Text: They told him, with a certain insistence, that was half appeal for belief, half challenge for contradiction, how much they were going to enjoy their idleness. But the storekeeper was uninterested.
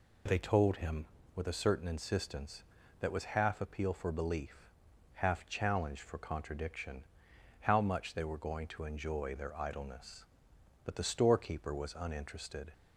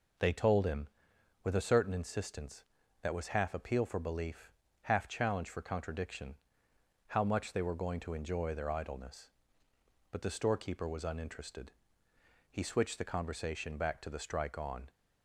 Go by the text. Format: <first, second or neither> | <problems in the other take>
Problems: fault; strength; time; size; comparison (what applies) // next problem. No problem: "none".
first | goes on to say "He switched the conversation back to the strike on"; strong; from 12.4 s on; 2.4 s long